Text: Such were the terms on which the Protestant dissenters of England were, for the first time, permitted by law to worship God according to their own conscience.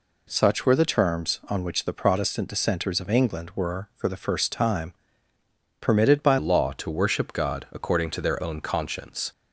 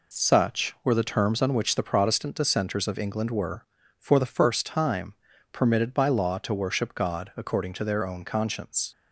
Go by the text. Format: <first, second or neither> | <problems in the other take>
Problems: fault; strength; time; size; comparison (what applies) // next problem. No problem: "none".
second | changes voice at "law"; from 6.3 s on; 3.0 s long